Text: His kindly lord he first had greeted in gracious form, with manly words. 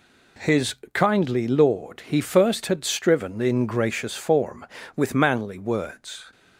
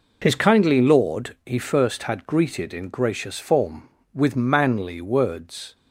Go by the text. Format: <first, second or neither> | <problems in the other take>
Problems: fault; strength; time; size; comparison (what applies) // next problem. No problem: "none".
second | pauses between "His" and "kindly"; slight; at 0.7 s; 0.18 s long // says "striven" for "greeted"; at 2.8 s